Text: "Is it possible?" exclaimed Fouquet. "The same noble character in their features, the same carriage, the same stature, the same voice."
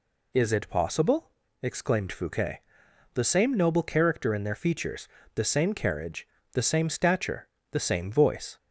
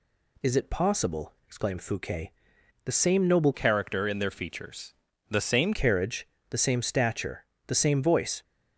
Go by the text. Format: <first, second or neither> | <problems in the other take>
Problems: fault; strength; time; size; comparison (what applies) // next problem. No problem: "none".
first | changes voice from "character" to "same"; from 3.5 to 5.7 s; 2.2 s long